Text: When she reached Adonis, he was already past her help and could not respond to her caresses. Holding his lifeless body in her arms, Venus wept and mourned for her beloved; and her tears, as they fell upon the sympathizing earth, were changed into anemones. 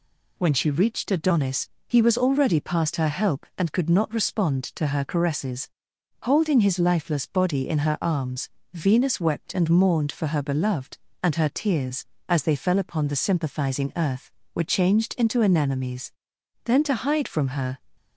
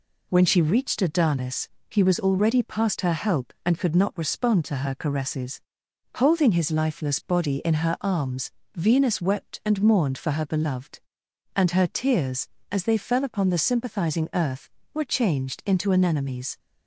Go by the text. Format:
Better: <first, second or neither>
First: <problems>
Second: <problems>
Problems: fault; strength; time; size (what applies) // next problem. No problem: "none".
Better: second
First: goes on to say "Then to hide from her"; noticeable; from 16.6 s on; 1.1 s long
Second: none